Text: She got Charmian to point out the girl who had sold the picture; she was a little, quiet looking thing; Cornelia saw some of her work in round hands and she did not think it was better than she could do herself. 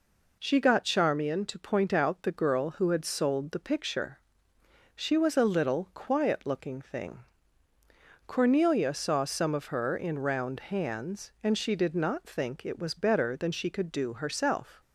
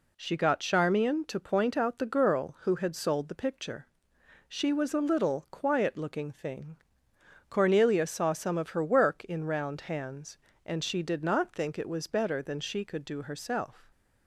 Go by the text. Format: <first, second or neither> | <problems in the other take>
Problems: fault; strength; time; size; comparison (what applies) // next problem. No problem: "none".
second | skips "work"; at 9.9 s